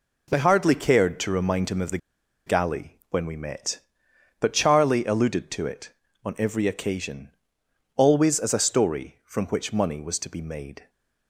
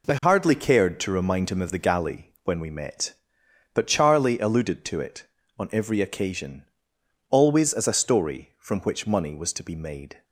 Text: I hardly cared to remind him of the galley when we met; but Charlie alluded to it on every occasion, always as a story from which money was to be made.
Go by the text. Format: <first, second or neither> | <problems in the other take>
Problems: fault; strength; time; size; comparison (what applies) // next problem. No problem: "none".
second | pauses between "the" and "galley"; noticeable; at 1.9 s; 0.49 s long